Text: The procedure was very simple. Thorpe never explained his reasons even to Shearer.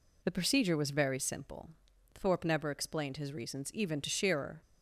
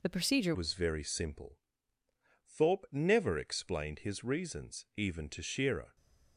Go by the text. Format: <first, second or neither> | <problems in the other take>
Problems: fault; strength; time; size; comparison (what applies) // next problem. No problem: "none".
first | changes voice at "was"; from 0.5 s on; 5.4 s long